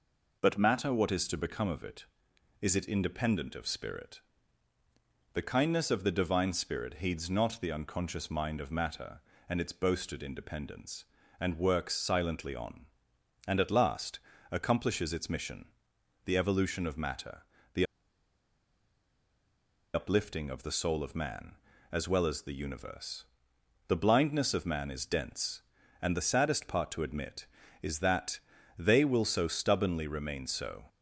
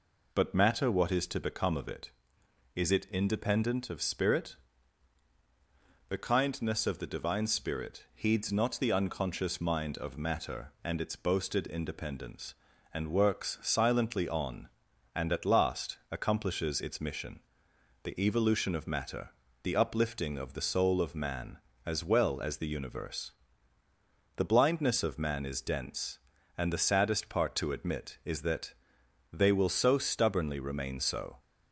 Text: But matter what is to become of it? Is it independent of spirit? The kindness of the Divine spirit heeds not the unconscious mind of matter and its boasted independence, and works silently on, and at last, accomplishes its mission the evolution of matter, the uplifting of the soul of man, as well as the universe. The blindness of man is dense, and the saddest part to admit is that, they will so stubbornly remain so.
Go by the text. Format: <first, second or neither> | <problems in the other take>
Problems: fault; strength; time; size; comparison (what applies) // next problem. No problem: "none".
second | pauses between "mission" and "the"; noticeable; at 15.6 s; 0.58 s long; noticeable in the second // pauses between "the" and "uplifting"; strong; at 17.8 s; 2.0 s long